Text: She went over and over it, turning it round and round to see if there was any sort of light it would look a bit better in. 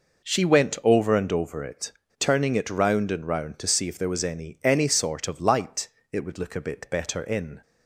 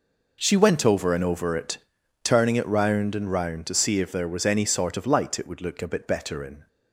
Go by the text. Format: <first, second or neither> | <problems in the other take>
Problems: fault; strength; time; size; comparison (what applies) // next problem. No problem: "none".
second | says "any" twice; at 4.6 s // pauses between "light" and "it"; slight; at 5.8 s; 0.24 s long